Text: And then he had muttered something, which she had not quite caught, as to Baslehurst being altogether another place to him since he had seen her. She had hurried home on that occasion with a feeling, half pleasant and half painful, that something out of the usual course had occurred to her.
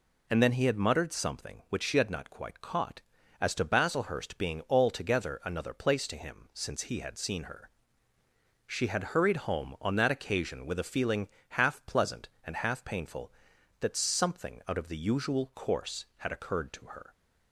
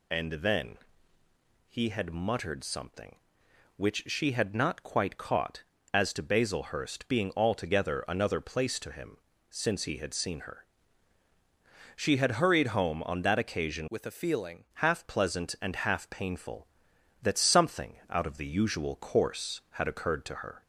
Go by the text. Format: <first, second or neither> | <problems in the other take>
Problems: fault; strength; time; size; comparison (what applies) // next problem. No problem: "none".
first | pauses between "then" and "he"; noticeable; at 0.7 s; 0.92 s long // pauses between "him" and "since"; slight; at 9.1 s; 0.34 s long // changes voice from "with" to "feeling"; from 13.8 to 14.6 s; 0.8 s long